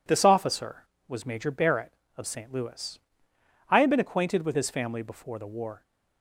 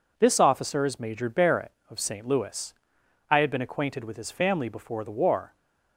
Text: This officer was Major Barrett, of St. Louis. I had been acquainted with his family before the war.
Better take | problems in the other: first | says "is" for "was"; at 0.8 s

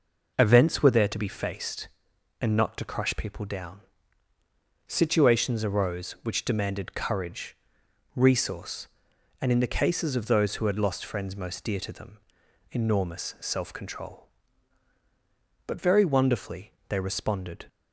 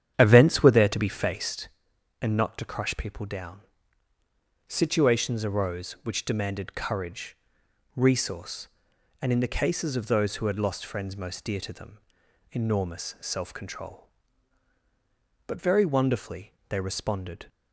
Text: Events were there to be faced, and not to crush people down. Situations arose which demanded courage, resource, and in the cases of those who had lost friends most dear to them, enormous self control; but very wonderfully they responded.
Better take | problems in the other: first | starts louder than the rest; strong; until 1.6 s; 9.5 dB // pauses between "wonderfully" and "they"; slight; at 16.5 s; 0.16 s long; slight in the first

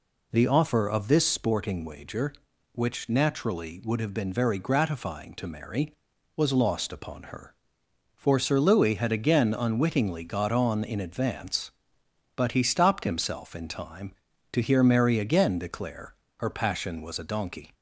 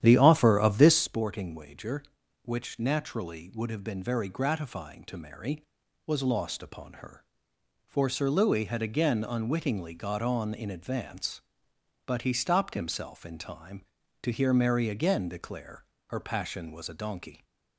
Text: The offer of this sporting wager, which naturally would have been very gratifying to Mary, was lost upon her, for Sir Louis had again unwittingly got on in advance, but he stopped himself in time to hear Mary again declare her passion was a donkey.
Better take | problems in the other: first | starts louder than the rest; strong; until 1.1 s; 10.5 dB // pauses between "declare" and "her"; slight; at 15.8 s; 0.24 s long; slight in the first

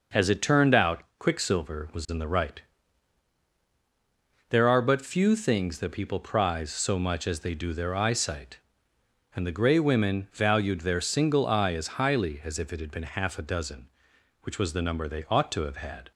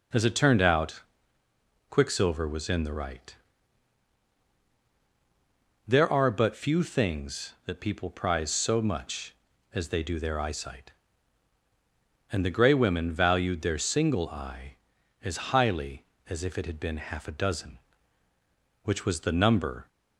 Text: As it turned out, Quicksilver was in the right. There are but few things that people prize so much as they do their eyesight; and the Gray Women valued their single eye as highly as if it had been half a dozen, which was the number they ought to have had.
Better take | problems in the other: first | stops before "they ought to have had"; at 19.8 s

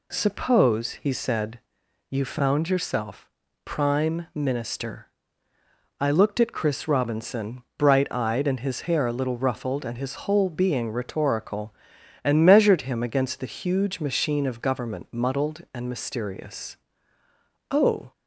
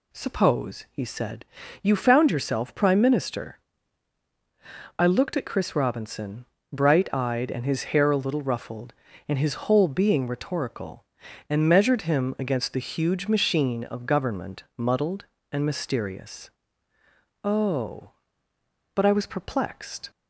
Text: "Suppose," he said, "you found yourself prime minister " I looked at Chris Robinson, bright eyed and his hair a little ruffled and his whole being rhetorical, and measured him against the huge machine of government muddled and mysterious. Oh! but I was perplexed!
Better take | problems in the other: second | pauses between "yourself" and "prime"; slight; at 3.3 s; 0.32 s long // stops before "but I was perplexed"; at 18.1 s

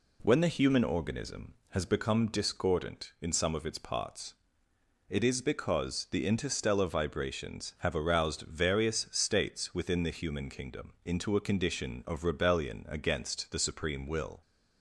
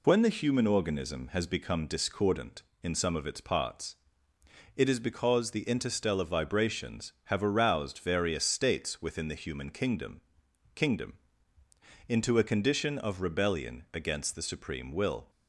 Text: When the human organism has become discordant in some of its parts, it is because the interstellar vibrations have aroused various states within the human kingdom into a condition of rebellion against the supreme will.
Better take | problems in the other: first | says "kingdom" twice; at 10.7 s

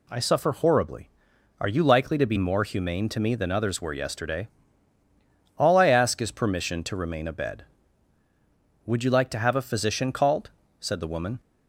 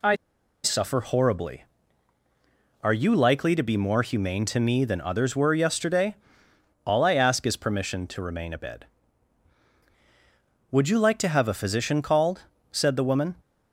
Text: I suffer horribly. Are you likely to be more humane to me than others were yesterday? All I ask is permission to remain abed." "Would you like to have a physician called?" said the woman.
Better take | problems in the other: first | pauses between "I" and "suffer"; noticeable; at 0.1 s; 0.49 s long

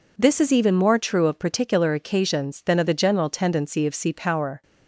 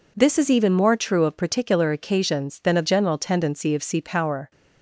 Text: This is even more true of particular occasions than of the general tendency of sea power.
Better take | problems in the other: first | skips "the"; at 2.8 s

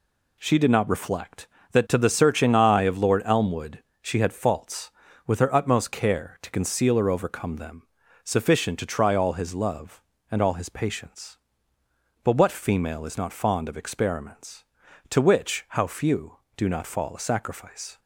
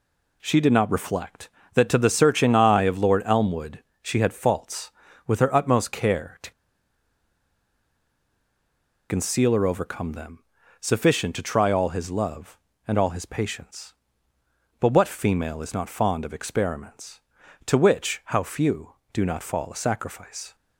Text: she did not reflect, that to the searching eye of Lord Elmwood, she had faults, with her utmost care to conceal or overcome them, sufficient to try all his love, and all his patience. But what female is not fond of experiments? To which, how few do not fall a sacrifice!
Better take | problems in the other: first | pauses between "to" and "conceal"; strong; at 6.5 s; 2.5 s long

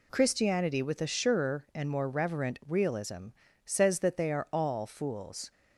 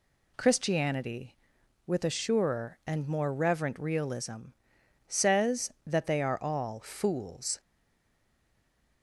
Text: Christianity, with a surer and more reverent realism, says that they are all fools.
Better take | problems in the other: first | stays silent after the last word; noticeable; from 7.5 s on; 1.5 s long

